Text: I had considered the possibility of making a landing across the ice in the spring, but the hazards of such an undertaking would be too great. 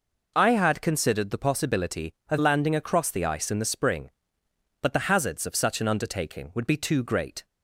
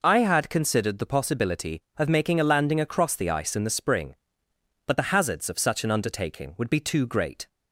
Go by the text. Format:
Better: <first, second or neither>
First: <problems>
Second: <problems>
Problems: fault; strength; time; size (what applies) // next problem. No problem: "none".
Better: second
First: skips "making a"; at 2.3 s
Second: none